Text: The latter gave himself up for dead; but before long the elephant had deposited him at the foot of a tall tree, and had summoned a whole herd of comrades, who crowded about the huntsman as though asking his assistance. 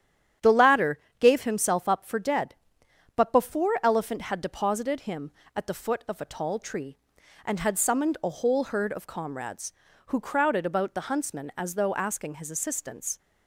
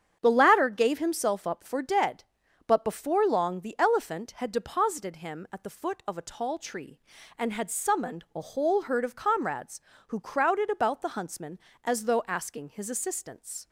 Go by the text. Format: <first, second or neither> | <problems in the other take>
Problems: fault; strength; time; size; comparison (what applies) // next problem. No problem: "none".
second | starts louder than the rest; strong; until 1.6 s; 9.5 dB; strong in the second // pauses between "latter" and "gave"; slight; at 0.9 s; 0.22 s long // skips "long the"; at 3.7 s